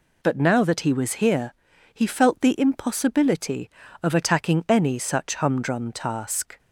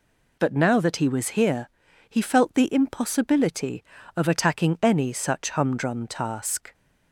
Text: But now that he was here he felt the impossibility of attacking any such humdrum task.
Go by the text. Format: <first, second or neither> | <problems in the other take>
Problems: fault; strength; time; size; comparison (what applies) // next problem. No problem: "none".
neither | pauses between "here" and "he"; the same in both